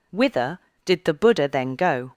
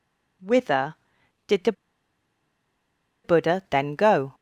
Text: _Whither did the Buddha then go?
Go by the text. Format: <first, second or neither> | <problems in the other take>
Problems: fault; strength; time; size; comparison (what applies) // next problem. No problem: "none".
first | pauses between "the" and "Buddha"; strong; at 1.7 s; 1.5 s long